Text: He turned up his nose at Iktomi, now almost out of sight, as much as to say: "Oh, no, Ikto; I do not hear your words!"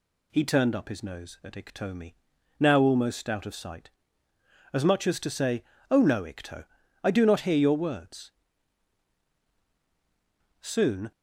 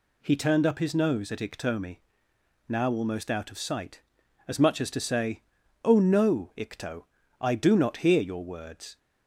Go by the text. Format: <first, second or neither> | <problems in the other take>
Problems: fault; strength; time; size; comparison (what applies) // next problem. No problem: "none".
second | goes on to say "Soon"; from 10.6 s on; 0.50 s long